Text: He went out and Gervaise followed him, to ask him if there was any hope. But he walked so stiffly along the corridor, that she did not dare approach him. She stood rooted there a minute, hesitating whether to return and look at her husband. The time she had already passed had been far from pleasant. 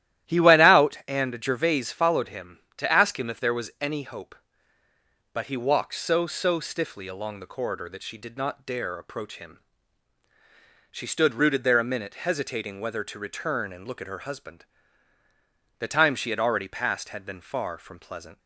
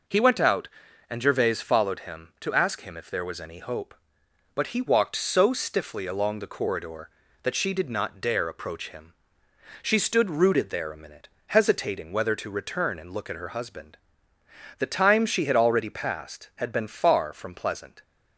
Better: second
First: starts louder than the rest; strong; until 1.3 s; 13 dB // says "so" twice; at 6.2 s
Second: none

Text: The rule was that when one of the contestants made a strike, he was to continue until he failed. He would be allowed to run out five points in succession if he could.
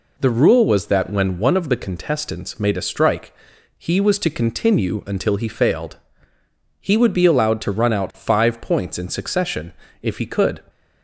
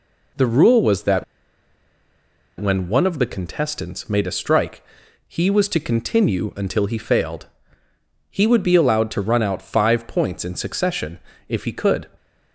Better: first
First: pauses between "succession" and "if"; slight; at 9.7 s; 0.30 s long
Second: pauses between "that" and "when"; strong; at 1.2 s; 1.3 s long // pauses between "succession" and "if"; slight; at 11.1 s; 0.30 s long

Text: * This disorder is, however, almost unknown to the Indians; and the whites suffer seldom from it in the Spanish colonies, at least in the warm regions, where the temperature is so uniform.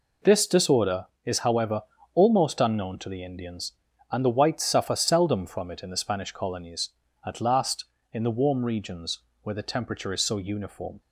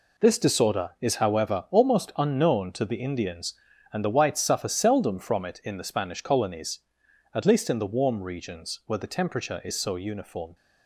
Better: second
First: says "last" for "least"; at 7.3 s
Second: none

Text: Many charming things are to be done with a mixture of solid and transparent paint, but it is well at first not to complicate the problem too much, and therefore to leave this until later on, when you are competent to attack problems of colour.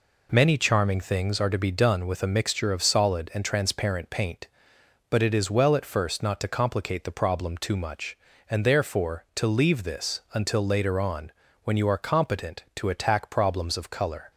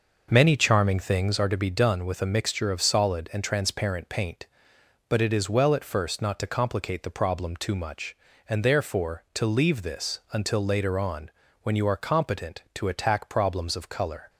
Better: first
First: none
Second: starts louder than the rest; noticeable; until 1.6 s; 6 dB

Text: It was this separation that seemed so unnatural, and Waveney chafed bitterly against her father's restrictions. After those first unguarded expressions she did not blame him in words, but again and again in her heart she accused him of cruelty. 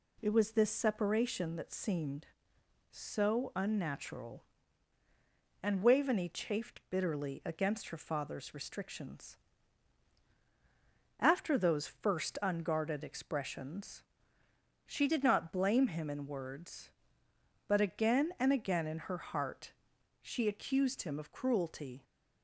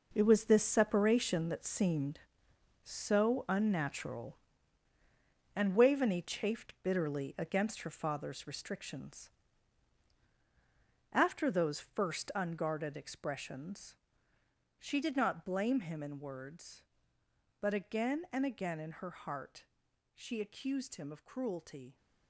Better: first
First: pauses between "expressions" and "she"; noticeable; at 14.0 s; 0.82 s long // pauses between "heart" and "she"; noticeable; at 19.7 s; 0.50 s long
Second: gets quieter; strong; throughout; 10 dB // pauses between "expressions" and "she"; noticeable; at 13.9 s; 0.82 s long // pauses between "heart" and "she"; noticeable; at 19.6 s; 0.50 s long

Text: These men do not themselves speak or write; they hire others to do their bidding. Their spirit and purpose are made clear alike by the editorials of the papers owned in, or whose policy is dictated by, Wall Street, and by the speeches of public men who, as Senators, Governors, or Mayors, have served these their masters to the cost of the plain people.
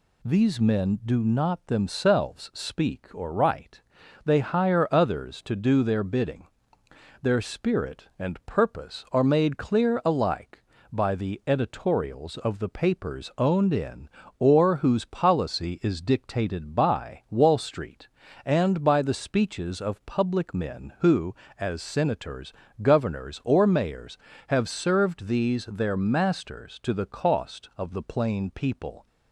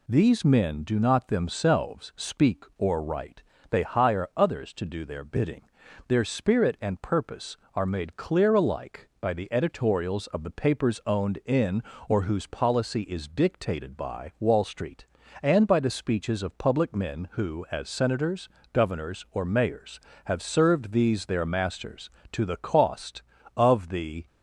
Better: first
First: none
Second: stops before "plain people"; at 24.2 s

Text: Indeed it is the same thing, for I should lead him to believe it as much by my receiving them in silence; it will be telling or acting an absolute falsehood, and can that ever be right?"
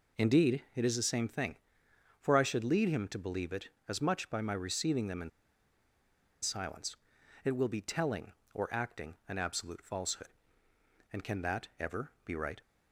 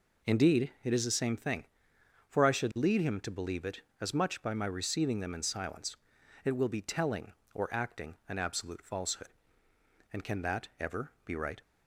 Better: second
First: pauses between "in" and "silence"; at 5.2 s; 1.1 s long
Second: none

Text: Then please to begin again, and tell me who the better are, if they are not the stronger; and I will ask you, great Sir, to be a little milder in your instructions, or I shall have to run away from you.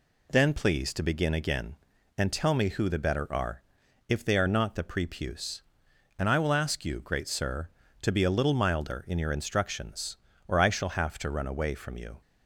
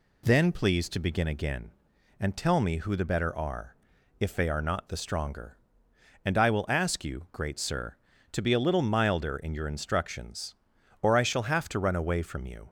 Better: second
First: says "prepuce" for "stronger"; at 4.8 s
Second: none

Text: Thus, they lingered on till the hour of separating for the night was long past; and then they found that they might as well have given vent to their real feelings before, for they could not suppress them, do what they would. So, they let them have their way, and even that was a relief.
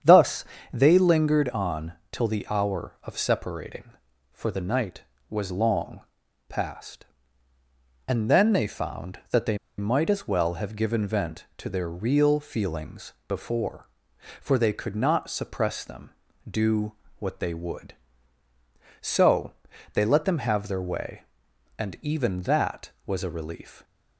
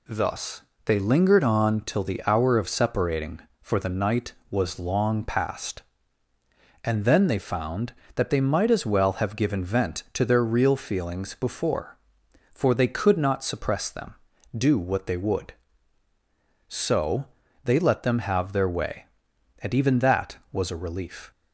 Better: second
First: starts louder than the rest; strong; until 1.3 s; 8.5 dB // pauses between "on" and "till"; slight; at 1.9 s; 0.18 s long // pauses between "long" and "past"; noticeable; at 6.0 s; 0.48 s long // pauses between "they" and "might"; slight; at 9.5 s; 0.21 s long // pauses between "feelings" and "before"; slight; at 13.1 s; 0.16 s long // pauses between "do" and "what"; slight; at 16.9 s; 0.26 s long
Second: none

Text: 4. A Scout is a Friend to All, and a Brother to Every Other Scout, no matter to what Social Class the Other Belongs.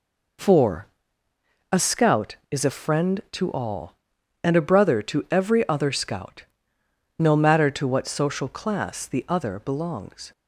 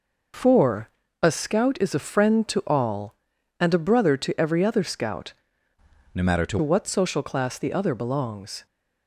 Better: first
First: none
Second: changes voice from "no" to "to"; from 6.1 to 6.5 s; 0.4 s long

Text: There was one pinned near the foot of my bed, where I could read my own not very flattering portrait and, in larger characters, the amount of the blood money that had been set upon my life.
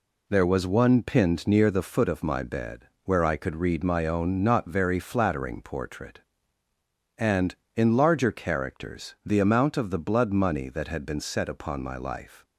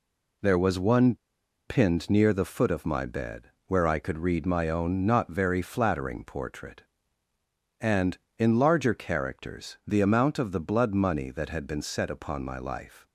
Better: first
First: none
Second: pauses between "one" and "pinned"; noticeable; at 1.1 s; 0.52 s long

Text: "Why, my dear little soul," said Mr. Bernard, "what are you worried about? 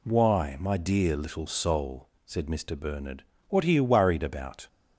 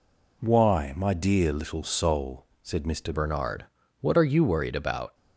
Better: first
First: none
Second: changes voice at "Bernard"; from 3.1 s on; 2.0 s long

